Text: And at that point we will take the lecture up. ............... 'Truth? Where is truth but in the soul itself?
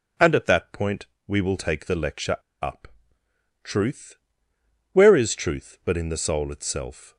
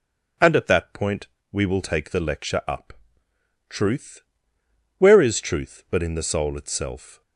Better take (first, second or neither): second